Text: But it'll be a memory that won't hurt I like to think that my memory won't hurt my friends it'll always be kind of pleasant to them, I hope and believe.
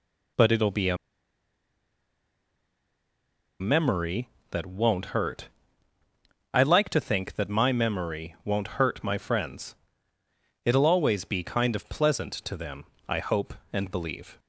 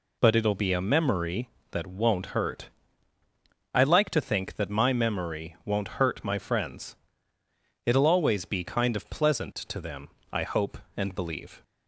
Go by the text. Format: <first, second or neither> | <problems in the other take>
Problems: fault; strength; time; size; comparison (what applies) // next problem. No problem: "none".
second | pauses between "a" and "memory"; strong; at 0.9 s; 2.6 s long // pauses between "hurt" and "I"; at 5.4 s; 1.0 s long; also in the second // pauses between "friends" and "it'll"; noticeable; at 9.7 s; 0.90 s long; noticeable in the second